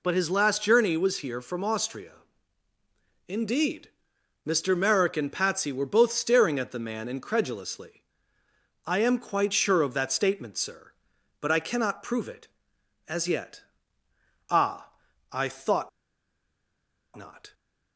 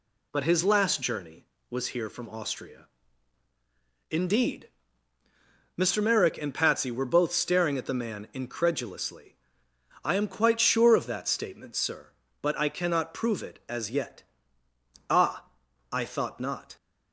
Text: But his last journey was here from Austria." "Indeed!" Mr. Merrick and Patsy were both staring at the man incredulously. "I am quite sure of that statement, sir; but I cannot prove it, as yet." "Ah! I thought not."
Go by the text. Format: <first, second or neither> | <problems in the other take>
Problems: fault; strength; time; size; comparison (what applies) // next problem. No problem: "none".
second | pauses between "thought" and "not"; strong; at 15.8 s; 1.2 s long